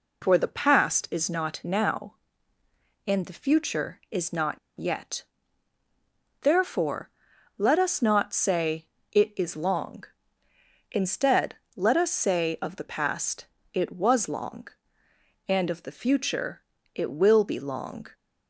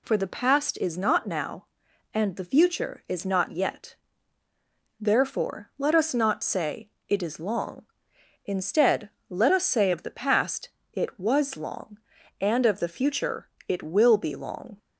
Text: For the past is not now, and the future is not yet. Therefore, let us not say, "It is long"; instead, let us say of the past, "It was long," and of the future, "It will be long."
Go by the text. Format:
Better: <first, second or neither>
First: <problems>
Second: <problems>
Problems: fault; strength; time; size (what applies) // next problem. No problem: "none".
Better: second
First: pauses between "not" and "yet"; slight; at 4.5 s; 0.23 s long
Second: none